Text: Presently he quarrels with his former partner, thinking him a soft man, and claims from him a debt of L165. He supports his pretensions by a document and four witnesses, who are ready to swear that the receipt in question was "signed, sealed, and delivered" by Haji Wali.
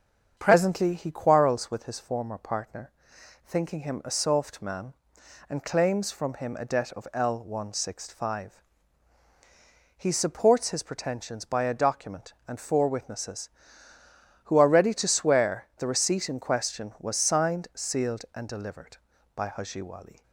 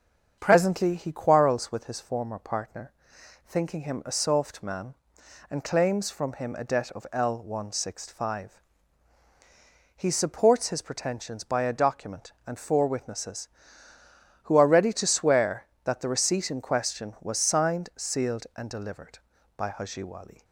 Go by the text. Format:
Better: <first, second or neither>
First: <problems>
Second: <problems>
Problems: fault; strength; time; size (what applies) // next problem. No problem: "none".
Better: second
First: starts louder than the rest; until 1.3 s; 7 dB // skips "that"; at 15.7 s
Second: starts louder than the rest; until 1.4 s; 7 dB